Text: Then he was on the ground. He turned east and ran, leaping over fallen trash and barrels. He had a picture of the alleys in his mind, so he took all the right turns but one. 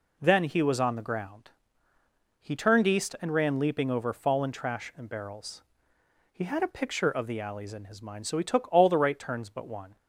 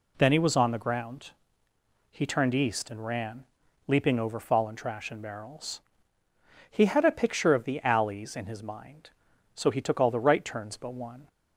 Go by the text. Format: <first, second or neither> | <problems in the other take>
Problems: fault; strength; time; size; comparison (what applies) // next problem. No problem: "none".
neither | none